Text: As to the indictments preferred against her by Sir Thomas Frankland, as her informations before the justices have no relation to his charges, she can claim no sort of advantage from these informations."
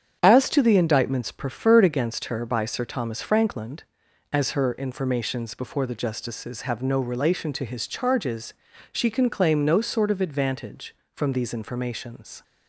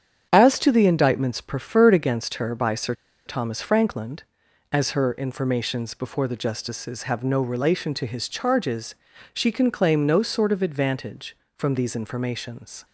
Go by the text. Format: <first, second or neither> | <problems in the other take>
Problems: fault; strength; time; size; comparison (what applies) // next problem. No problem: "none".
first | starts louder than the rest; strong; until 1.3 s; 8.5 dB; strong in the first // pauses between "Sir" and "Thomas"; slight; at 2.9 s; 0.33 s long